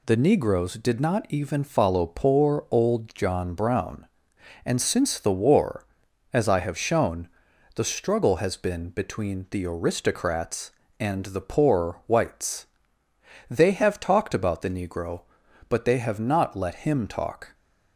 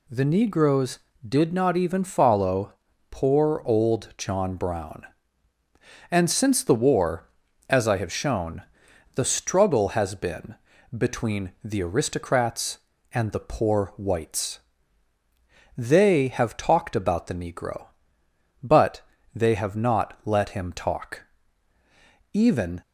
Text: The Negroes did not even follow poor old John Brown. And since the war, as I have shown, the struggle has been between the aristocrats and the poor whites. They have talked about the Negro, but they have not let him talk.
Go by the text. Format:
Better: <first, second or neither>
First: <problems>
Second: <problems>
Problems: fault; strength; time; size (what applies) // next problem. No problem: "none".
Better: first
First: none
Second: pauses between "follow" and "poor"; at 2.7 s; 0.38 s long // pauses between "been" and "between"; at 10.5 s; 0.42 s long // pauses between "but" and "they"; slight; at 19.0 s; 0.34 s long // goes on to say "Even"; slight; from 22.3 s on; 0.48 s long